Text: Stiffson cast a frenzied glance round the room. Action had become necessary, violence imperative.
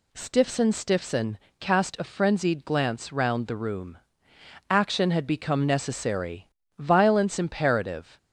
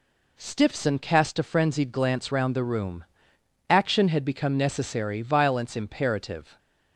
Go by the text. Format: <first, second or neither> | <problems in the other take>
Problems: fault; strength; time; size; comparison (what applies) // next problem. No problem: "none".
second | says "Stiffson" twice; at 0.7 s